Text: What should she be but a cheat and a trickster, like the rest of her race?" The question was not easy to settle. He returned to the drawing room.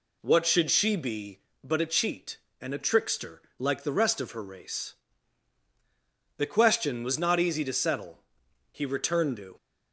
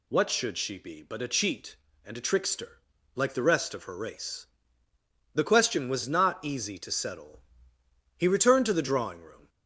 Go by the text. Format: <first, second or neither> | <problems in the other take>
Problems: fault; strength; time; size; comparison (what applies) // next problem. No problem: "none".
second | stops before "the drawing room"; at 9.5 s